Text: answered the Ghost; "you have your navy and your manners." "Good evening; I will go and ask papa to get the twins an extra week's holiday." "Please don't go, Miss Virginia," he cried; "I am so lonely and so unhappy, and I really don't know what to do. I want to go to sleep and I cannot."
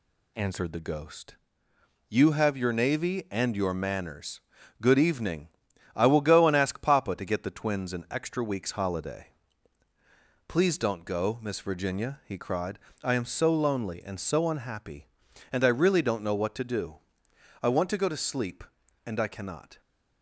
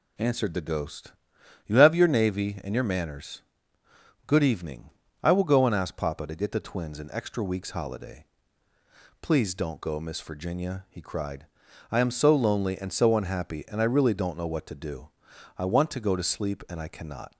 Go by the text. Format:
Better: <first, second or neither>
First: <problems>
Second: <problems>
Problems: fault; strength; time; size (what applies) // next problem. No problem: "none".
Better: neither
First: none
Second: none